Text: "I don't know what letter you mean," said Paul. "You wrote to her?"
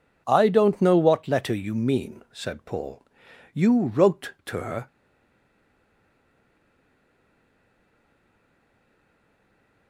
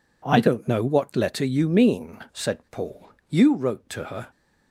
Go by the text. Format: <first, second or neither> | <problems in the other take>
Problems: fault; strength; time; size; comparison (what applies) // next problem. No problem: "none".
second | stays silent after the last word; strong; from 4.8 s on; 5.0 s long